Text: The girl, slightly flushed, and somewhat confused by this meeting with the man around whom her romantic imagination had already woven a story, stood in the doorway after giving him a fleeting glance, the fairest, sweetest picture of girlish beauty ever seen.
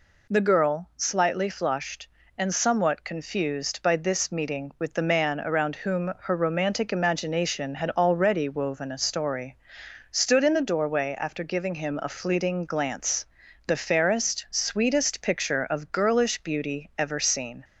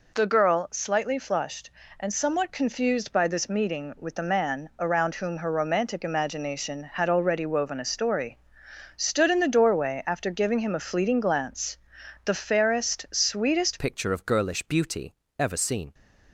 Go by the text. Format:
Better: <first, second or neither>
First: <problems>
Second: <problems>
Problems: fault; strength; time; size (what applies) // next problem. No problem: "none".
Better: first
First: none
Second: changes voice at "picture"; from 13.7 s on; 2.2 s long // pauses between "beauty" and "ever"; slight; at 15.1 s; 0.26 s long